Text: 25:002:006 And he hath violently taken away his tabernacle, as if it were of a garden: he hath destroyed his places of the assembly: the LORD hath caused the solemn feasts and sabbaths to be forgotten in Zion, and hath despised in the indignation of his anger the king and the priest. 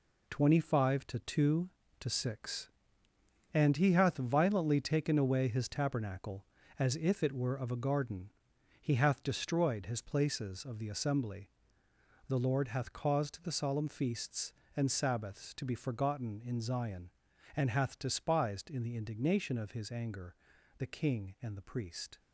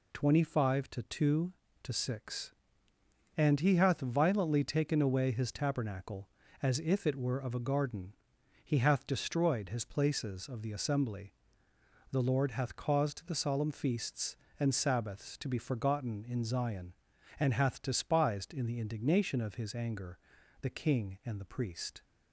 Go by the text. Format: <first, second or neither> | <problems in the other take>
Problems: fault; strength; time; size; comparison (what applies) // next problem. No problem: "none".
second | gets quieter; strong; throughout; 8.5 dB // pauses between "anger" and "the"; at 20.3 s; 0.42 s long; also in the second